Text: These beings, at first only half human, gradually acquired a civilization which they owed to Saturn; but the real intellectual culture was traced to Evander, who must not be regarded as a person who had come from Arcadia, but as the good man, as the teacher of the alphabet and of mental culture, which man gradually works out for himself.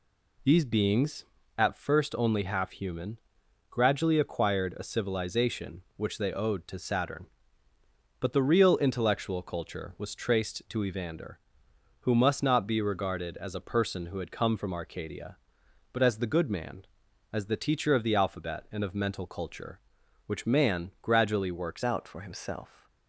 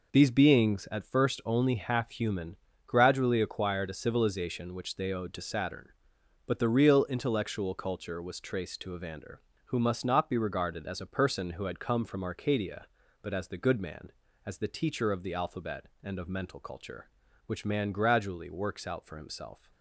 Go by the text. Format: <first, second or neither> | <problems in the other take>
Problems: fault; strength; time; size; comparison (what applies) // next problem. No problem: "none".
second | changes voice at "out"; from 21.8 s on; 1.0 s long